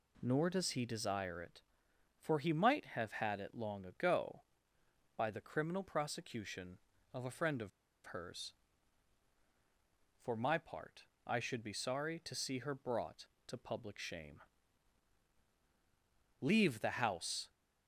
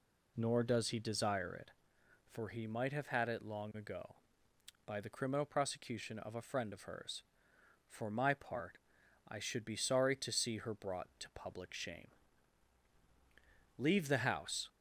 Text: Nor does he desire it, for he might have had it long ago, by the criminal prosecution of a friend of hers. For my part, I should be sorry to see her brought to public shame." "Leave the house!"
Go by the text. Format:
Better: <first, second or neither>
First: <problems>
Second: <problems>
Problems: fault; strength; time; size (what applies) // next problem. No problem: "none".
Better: second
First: pauses between "of" and "hers"; slight; at 7.6 s; 0.36 s long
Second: none